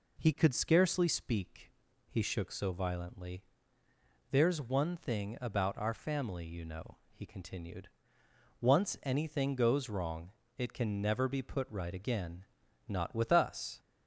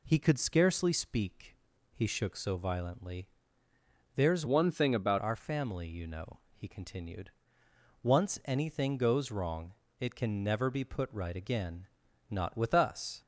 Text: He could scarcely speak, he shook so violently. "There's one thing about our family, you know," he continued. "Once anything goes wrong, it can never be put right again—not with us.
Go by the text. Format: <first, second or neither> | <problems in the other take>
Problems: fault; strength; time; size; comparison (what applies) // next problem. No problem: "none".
first | changes voice from "one" to "about"; from 4.4 to 5.1 s; 0.7 s long